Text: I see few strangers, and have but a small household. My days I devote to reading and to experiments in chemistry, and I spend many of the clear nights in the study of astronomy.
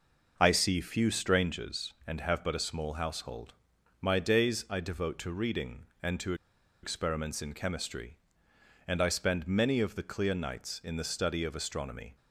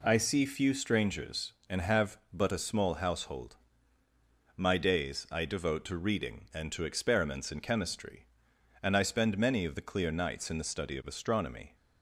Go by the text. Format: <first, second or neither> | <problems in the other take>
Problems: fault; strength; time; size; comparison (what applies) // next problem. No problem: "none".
second | pauses between "to" and "experiments"; noticeable; at 6.3 s; 0.49 s long